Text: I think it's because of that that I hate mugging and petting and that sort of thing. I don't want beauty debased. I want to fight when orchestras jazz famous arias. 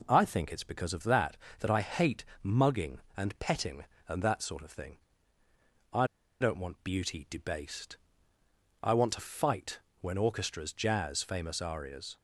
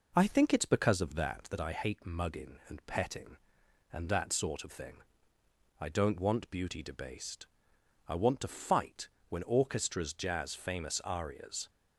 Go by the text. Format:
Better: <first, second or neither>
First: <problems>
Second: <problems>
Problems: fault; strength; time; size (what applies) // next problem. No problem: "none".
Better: second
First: pauses between "hate" and "mugging"; slight; at 2.2 s; 0.18 s long // pauses between "I" and "don't"; slight; at 6.0 s; 0.33 s long // pauses between "fight" and "when"; slight; at 9.7 s; 0.22 s long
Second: pauses between "fight" and "when"; slight; at 9.0 s; 0.22 s long